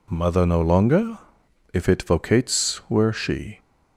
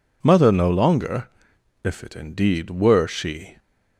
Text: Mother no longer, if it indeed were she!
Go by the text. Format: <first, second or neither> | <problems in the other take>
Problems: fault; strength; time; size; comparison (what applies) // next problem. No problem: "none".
second | says "vocates" for "indeed"; at 2.0 s